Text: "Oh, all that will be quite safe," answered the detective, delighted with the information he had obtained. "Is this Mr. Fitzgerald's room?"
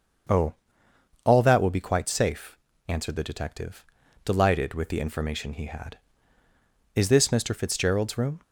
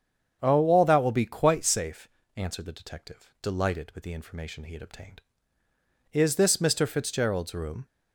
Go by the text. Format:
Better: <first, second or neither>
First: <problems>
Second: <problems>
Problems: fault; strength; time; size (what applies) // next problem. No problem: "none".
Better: second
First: starts louder than the rest; until 2.0 s; 6.5 dB // skips "obtained"; at 6.4 s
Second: starts louder than the rest; strong; until 1.4 s; 7.5 dB